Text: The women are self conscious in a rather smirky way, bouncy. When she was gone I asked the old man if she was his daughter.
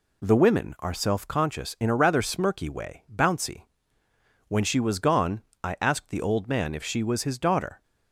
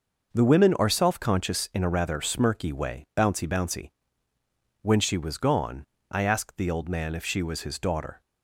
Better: first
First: pauses between "gone" and "I"; slight; at 5.4 s; 0.20 s long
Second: says "bouncy" twice; at 3.4 s // pauses between "gone" and "I"; slight; at 5.8 s; 0.26 s long

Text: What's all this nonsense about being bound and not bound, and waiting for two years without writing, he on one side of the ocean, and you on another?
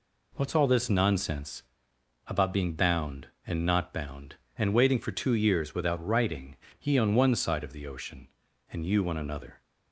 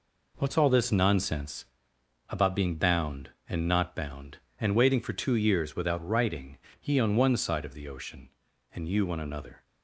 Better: first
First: pauses between "nonsense" and "about"; noticeable; at 1.6 s; 0.64 s long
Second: gets quieter; strong; throughout; 8 dB // pauses between "nonsense" and "about"; noticeable; at 1.6 s; 0.64 s long

